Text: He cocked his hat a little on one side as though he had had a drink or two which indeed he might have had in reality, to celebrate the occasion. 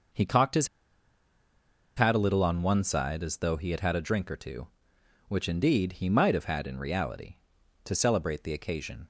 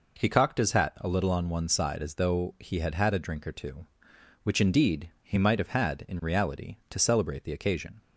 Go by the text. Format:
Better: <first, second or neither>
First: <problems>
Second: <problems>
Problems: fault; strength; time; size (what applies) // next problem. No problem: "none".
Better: second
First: pauses between "his" and "hat"; strong; at 0.6 s; 1.2 s long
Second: none